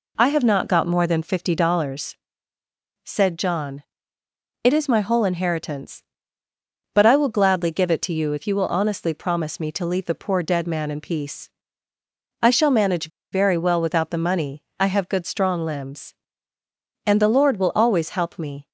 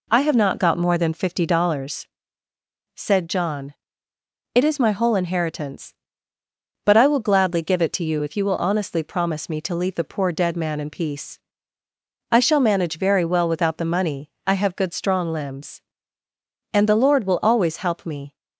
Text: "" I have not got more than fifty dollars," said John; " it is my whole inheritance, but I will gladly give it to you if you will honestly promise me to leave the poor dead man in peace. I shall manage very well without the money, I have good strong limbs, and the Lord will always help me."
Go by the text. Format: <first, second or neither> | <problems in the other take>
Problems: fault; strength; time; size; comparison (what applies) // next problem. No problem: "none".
second | pauses between "manage" and "very"; slight; at 13.1 s; 0.22 s long